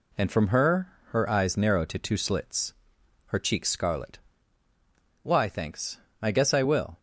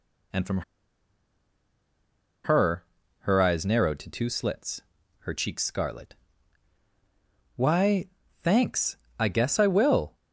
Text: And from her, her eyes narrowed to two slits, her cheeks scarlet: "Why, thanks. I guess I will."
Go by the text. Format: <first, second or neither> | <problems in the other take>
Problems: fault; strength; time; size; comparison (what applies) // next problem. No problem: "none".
first | pauses between "from" and "her"; strong; at 0.5 s; 1.8 s long